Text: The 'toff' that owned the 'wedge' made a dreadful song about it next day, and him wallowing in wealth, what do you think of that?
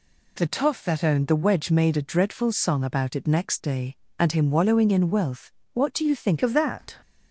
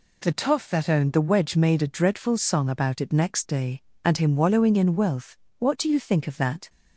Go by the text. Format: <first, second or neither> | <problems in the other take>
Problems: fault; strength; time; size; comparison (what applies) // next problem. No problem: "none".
second | changes voice at "of"; from 6.4 s on; 0.5 s long